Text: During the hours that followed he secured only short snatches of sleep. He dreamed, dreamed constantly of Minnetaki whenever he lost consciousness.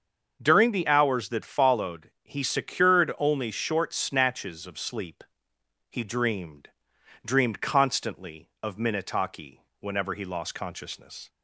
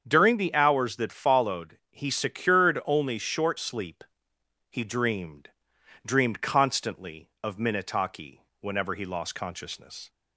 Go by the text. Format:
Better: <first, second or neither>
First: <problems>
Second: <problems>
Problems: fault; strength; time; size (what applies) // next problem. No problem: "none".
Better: first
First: starts louder than the rest; until 1.4 s; 6.5 dB // pauses between "Minnetaki" and "whenever"; slight; at 9.6 s; 0.18 s long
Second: starts louder than the rest; strong; until 1.0 s; 7.5 dB // skips "snatches of"; at 3.5 s // pauses between "Minnetaki" and "whenever"; slight; at 8.4 s; 0.18 s long